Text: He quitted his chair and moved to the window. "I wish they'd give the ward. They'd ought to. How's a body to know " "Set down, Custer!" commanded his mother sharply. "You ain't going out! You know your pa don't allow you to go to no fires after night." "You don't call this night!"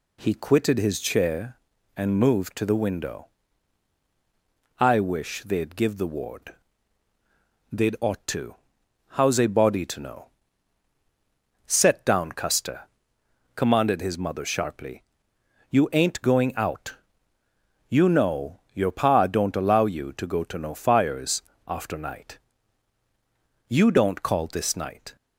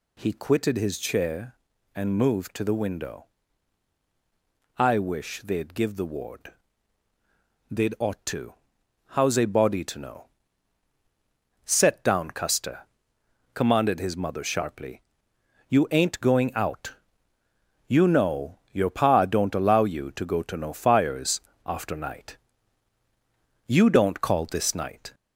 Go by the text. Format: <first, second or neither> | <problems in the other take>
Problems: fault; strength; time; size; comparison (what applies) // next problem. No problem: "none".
first | gets louder; throughout; 4 dB // pauses between "fires" and "after"; slight; at 21.3 s; 0.24 s long; slight in the first